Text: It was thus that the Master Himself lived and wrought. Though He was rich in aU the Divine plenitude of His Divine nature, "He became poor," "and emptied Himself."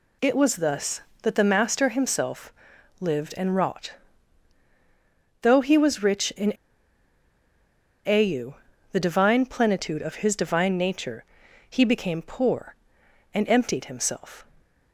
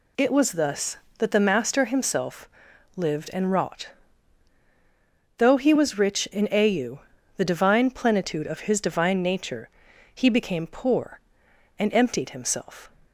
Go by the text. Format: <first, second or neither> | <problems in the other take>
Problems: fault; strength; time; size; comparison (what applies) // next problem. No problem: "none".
second | pauses between "Himself" and "lived"; noticeable; at 2.5 s; 0.46 s long; noticeable in the second // pauses between "in" and "aU"; strong; at 6.5 s; 1.5 s long // pauses between "aU" and "the"; slight; at 8.5 s; 0.36 s long; slight in the second